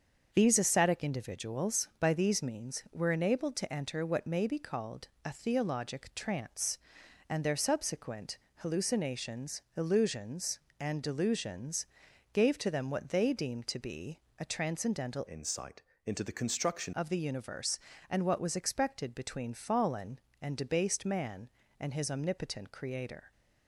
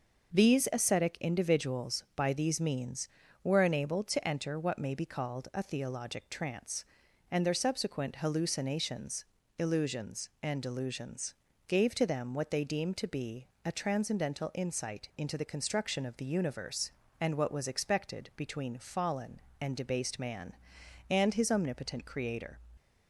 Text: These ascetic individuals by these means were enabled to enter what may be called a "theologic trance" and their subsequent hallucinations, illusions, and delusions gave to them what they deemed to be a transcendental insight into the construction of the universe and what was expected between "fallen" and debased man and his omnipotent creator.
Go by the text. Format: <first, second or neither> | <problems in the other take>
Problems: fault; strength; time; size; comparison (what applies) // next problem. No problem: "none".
second | starts louder than the rest; until 1.3 s; 7 dB; noticeable in the second // pauses between "called" and "a"; slight; at 5.0 s; 0.18 s long // pauses between "subsequent" and "hallucinations"; slight; at 8.3 s; 0.22 s long // pauses between "delusions" and "gave"; noticeable; at 11.8 s; 0.46 s long; slight in the second // pauses between "be" and "a"; slight; at 14.1 s; 0.18 s long; slight in the second // changes voice from "insight" to "construction"; from 15.2 to 16.9 s; 1.7 s long // pauses between "insight" and "into"; slight; at 15.8 s; 0.24 s long